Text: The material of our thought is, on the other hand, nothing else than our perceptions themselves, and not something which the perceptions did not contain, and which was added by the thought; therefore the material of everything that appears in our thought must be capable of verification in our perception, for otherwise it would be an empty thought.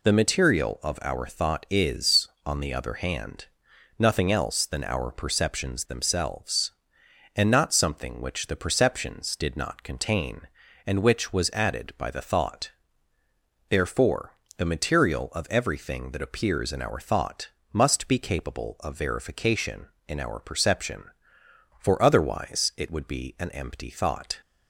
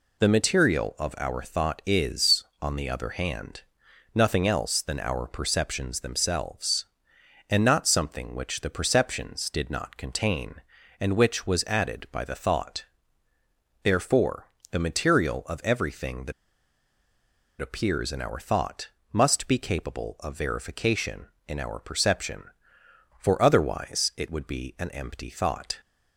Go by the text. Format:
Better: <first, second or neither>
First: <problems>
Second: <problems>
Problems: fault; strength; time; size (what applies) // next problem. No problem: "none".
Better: first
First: pauses between "therefore" and "the"; slight; at 14.3 s; 0.26 s long // pauses between "thought" and "must"; slight; at 17.4 s; 0.24 s long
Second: pauses between "therefore" and "the"; slight; at 14.4 s; 0.26 s long // pauses between "that" and "appears"; strong; at 16.3 s; 1.2 s long // pauses between "thought" and "must"; slight; at 18.8 s; 0.24 s long